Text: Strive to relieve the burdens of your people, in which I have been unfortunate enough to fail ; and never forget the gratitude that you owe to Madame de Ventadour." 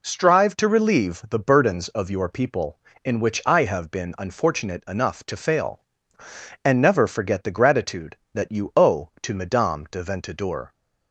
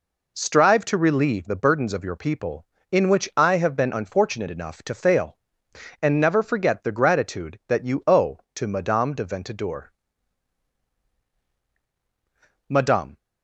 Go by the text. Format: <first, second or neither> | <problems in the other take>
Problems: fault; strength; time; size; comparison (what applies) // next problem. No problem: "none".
first | goes on to say "Madame"; slight; from 12.6 s on; 0.48 s long